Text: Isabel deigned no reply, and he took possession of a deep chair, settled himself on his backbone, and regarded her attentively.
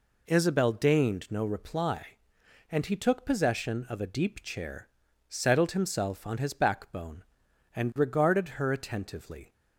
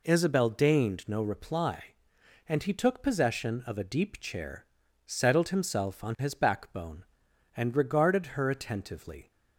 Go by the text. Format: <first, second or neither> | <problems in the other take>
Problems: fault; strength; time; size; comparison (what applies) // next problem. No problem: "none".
neither | none